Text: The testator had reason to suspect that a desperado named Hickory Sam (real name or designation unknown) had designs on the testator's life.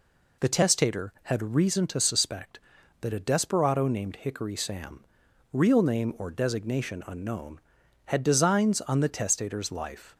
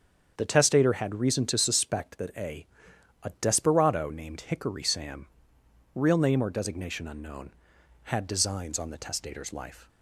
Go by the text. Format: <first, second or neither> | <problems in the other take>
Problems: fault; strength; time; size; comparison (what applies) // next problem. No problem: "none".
first | starts louder than the rest; strong; until 1.3 s; 7.5 dB // says "a" twice; at 3.2 s